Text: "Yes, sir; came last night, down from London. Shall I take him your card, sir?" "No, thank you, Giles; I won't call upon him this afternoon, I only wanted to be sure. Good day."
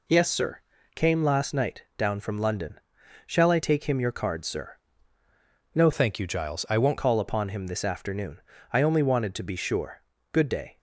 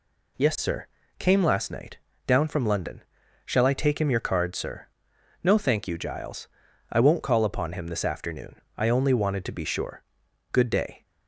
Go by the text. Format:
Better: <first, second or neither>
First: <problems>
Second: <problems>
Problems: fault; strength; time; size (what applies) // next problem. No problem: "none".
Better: second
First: changes voice from "thank" to "won't"; from 5.9 to 6.9 s; 1.0 s long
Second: none